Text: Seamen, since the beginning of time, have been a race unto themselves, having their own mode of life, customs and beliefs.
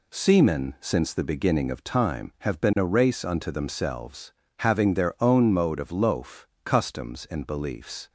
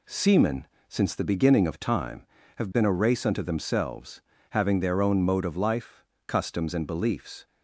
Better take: second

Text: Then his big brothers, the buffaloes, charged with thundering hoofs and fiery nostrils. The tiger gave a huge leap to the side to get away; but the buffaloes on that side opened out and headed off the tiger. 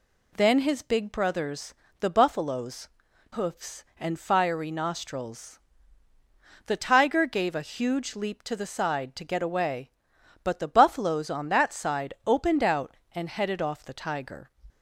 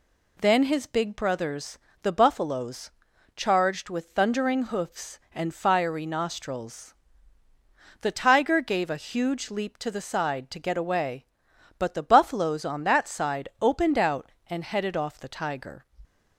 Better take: second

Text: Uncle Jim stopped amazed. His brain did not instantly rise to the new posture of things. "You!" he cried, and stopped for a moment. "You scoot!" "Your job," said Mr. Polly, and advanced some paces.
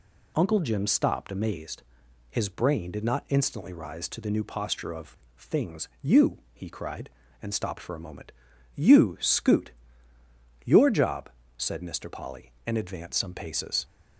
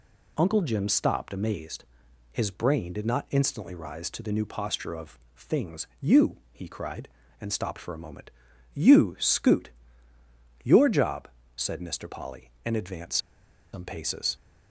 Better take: first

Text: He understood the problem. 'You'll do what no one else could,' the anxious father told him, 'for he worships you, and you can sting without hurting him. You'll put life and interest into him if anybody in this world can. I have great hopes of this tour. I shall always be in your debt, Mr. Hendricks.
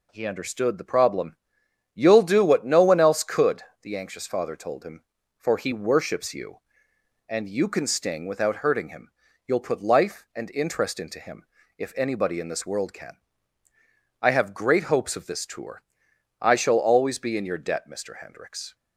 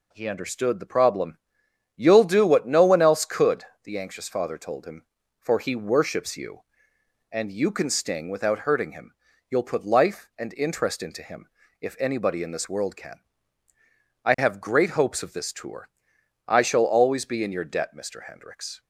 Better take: neither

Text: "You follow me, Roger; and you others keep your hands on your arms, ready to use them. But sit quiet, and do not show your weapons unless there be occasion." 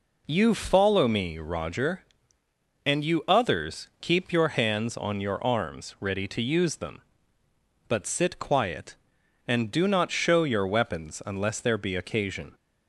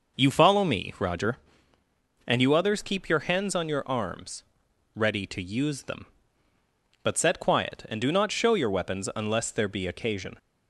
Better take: first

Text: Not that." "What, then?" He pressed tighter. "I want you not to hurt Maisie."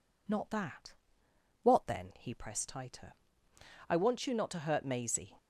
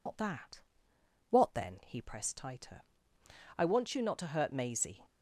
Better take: first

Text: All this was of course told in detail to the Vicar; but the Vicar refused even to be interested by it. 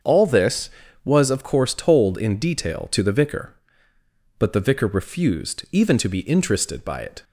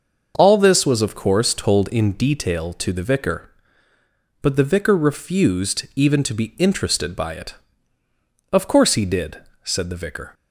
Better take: first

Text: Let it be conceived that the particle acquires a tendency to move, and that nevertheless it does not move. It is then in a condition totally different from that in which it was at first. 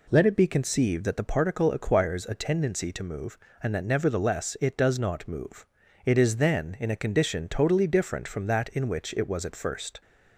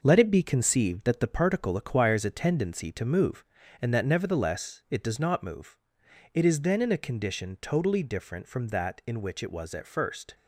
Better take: first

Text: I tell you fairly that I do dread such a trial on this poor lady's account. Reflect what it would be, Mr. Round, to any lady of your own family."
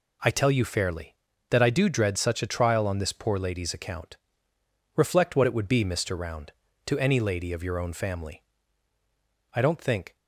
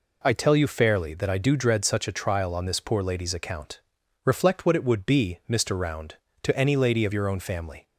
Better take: second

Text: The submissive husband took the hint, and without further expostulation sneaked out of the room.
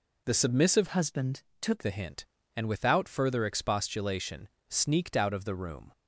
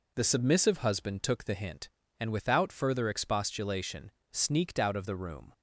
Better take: second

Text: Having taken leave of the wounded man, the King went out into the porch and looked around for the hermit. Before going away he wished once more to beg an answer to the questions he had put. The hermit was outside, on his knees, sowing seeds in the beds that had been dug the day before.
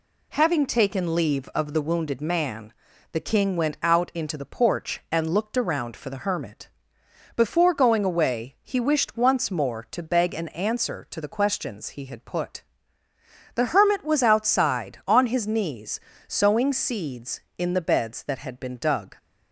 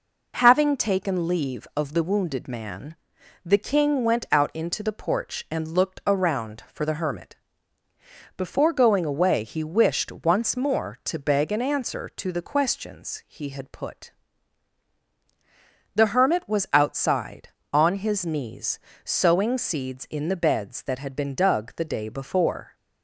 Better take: second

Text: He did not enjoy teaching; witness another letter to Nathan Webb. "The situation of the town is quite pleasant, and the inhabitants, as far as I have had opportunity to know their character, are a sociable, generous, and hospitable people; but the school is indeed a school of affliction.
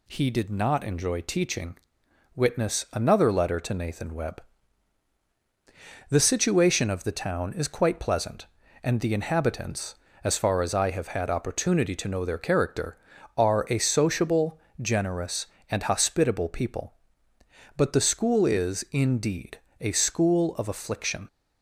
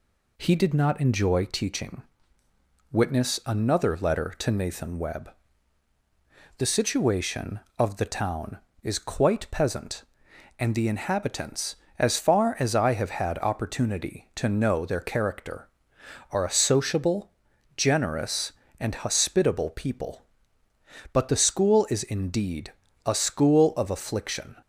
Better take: first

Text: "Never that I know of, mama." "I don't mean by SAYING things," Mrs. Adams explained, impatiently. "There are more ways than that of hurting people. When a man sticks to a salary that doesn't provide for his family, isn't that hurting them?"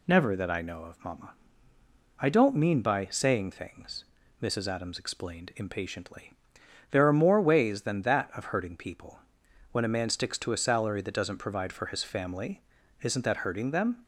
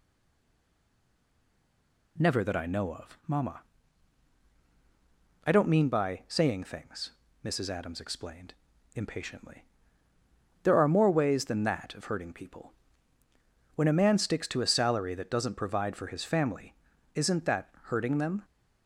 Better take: first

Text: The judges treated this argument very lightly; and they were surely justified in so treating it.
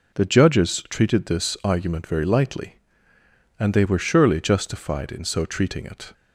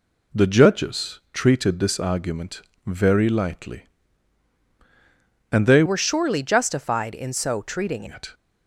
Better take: first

